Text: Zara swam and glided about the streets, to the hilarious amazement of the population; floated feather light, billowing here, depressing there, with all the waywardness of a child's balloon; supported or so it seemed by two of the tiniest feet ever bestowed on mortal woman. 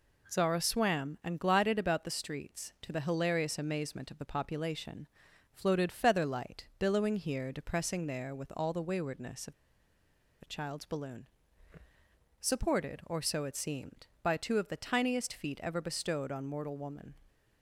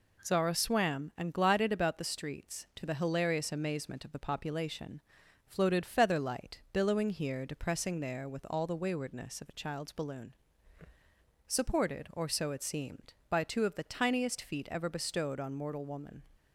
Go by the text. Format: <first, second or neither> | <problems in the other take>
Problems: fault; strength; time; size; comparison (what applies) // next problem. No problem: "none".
second | pauses between "of" and "a"; noticeable; at 9.5 s; 0.88 s long